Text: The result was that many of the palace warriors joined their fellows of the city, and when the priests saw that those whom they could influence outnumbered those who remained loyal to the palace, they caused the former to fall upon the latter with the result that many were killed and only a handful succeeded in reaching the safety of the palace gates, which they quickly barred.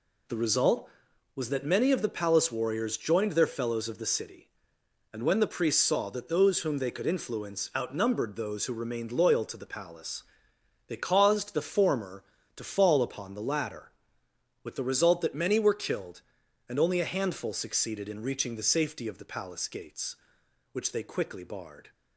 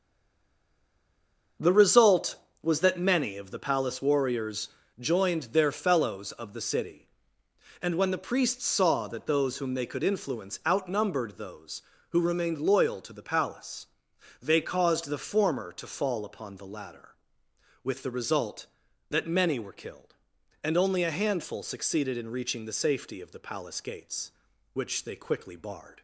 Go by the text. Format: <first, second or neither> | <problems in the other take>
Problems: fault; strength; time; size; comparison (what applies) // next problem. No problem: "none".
first | stays silent before the first word; noticeable; until 1.5 s; 1.5 s long // starts louder than the rest; until 2.8 s; 6.5 dB // pauses between "warriors" and "joined"; slight; at 4.6 s; 0.28 s long